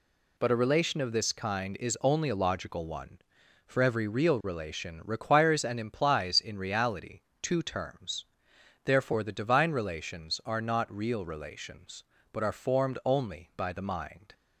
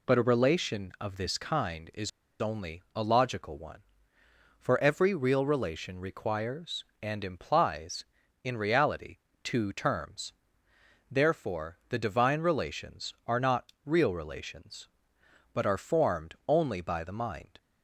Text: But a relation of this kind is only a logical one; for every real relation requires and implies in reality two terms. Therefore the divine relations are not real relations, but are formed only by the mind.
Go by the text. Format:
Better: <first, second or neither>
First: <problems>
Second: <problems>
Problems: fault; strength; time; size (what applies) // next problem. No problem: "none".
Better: first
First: pauses between "reality" and "two"; slight; at 7.2 s; 0.22 s long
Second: pauses between "is" and "only"; slight; at 2.0 s; 0.31 s long // pauses between "reality" and "two"; slight; at 9.1 s; 0.24 s long